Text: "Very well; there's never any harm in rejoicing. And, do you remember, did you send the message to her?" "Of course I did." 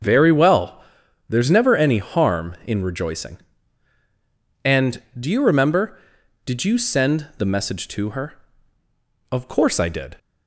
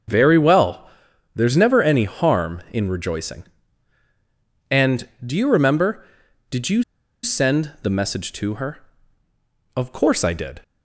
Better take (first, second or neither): first